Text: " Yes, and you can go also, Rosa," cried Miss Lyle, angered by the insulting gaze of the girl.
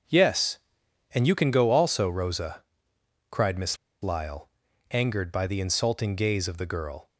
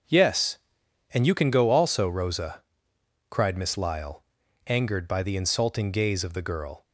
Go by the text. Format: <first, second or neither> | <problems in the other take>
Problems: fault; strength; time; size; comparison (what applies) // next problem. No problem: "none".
second | starts louder than the rest; until 1.6 s; 7 dB; also in the second // pauses between "Miss" and "Lyle"; slight; at 3.7 s; 0.26 s long